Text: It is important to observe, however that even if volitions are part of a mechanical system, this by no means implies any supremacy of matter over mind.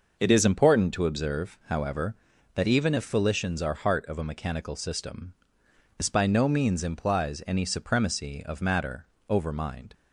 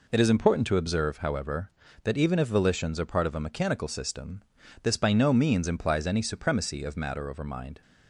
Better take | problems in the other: second | says "heart" for "part"; at 3.7 s // pauses between "matter" and "over"; slight; at 9.0 s; 0.24 s long

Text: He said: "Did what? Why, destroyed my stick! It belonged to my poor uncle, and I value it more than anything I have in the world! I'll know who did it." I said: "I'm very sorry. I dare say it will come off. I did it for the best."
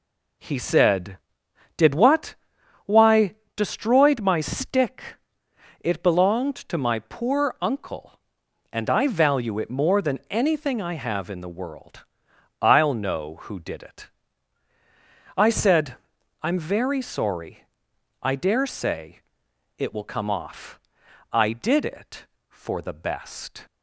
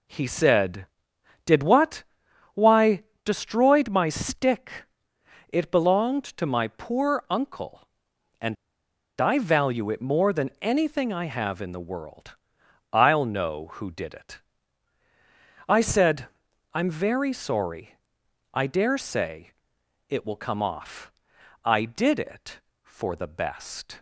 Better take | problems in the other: first | pauses between "and" and "I"; noticeable; at 8.5 s; 0.64 s long // pauses between "say" and "it"; noticeable; at 19.5 s; 0.56 s long; noticeable in the first

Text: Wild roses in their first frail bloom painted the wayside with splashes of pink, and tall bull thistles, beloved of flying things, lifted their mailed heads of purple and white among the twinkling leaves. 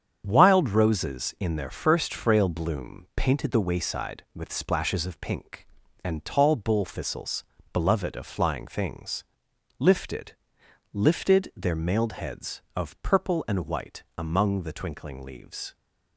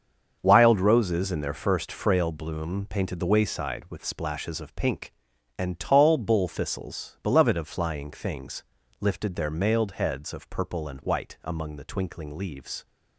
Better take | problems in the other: second | starts louder than the rest; strong; until 1.2 s; 8 dB; also in the second // says "lifted" twice; at 10.9 s // pauses between "white" and "among"; slight; at 14.0 s; 0.16 s long

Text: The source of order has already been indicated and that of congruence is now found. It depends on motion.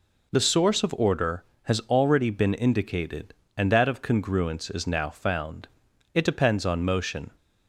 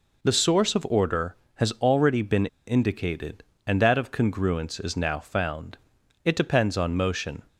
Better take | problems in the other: first | pauses between "been" and "indicated"; slight; at 2.4 s; 0.20 s long

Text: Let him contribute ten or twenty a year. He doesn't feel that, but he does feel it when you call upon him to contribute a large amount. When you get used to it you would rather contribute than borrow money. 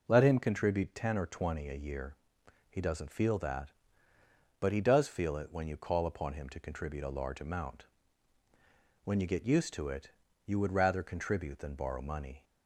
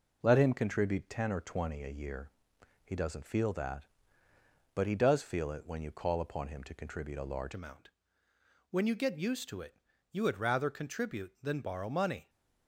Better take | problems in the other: first | changes voice at "amount"; from 7.5 s on; 4.7 s long // pauses between "it" and "you"; slight; at 9.7 s; 0.34 s long; slight in the first

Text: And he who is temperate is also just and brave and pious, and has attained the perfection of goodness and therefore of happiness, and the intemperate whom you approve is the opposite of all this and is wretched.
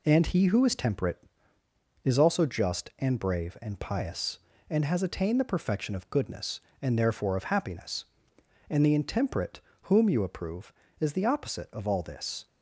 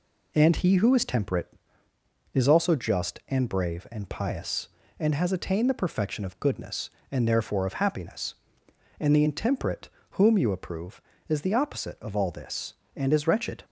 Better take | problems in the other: second | pauses between "intemperate" and "whom"; slight; at 9.6 s; 0.22 s long; slight in the second // stops before "and is wretched"; at 12.4 s

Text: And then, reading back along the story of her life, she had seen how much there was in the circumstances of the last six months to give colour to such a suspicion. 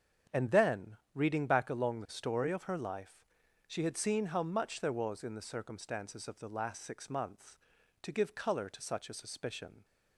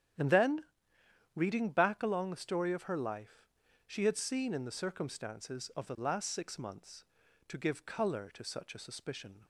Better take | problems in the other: first | starts louder than the rest; strong; until 1.8 s; 10.5 dB; strong in the first // skips "how much there was"; at 4.5 s

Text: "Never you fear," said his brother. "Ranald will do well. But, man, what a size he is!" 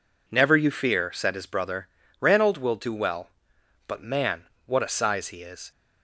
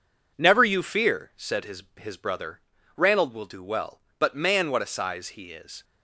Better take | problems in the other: first | says "his" twice; at 1.9 s

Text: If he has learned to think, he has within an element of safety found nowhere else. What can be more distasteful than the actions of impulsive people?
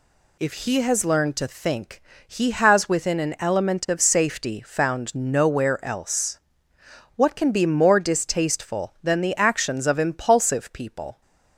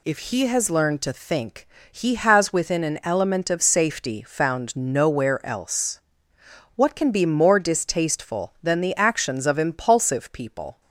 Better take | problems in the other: neither | none

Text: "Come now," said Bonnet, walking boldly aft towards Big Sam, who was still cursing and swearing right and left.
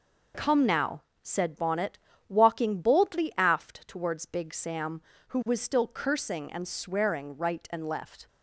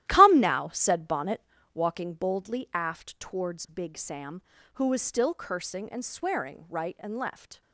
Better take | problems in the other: first | starts louder than the rest; strong; until 1.9 s; 13.5 dB

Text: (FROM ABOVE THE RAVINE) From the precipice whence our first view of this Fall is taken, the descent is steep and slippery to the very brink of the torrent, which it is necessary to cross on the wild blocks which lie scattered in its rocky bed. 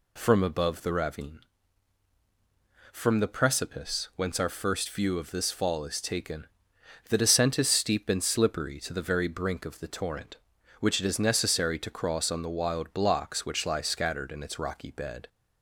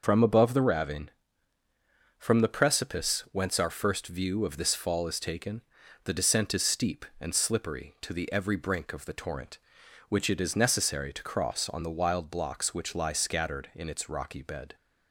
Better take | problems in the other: first | says "every" for "very"; at 8.3 s

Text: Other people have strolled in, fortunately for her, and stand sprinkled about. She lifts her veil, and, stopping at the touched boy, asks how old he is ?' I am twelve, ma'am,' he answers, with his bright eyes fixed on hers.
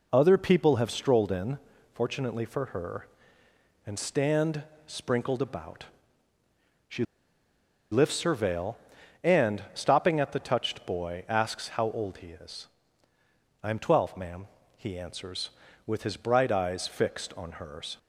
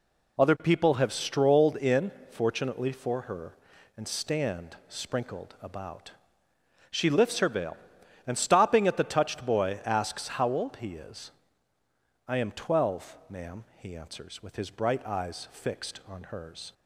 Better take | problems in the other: second | pauses between "stand" and "sprinkled"; slight; at 4.6 s; 0.22 s long // pauses between "She" and "lifts"; noticeable; at 7.0 s; 0.88 s long

